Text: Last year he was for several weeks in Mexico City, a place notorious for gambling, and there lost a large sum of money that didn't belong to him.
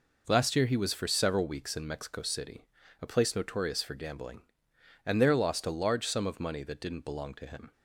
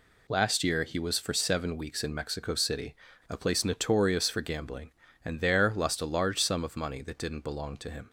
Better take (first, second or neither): first